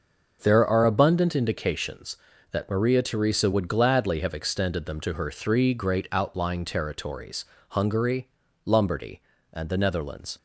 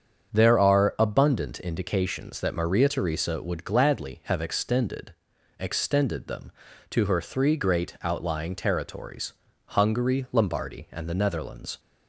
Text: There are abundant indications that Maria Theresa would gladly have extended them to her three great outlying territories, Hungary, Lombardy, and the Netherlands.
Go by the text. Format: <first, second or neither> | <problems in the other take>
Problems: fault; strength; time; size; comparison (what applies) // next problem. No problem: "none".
first | starts louder than the rest; strong; until 1.3 s; 7.5 dB; also in the first // says "extended" twice; at 5.6 s